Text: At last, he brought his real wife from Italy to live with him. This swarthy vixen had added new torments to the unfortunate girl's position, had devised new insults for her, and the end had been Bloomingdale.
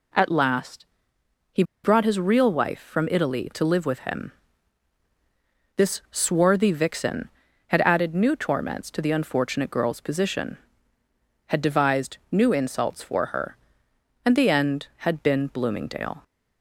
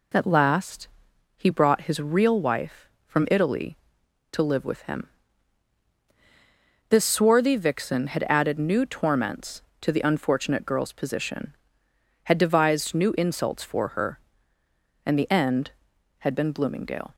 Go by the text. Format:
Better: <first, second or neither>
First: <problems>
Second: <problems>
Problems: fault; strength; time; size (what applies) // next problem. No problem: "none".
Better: second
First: pauses between "he" and "brought"; slight; at 1.6 s; 0.21 s long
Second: none